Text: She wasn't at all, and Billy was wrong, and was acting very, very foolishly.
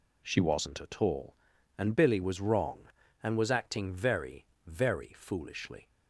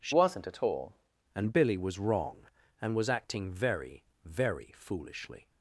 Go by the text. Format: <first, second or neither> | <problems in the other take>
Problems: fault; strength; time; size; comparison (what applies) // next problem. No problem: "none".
first | changes voice from "wasn't" to "all"; from 0.1 to 0.9 s; 0.8 s long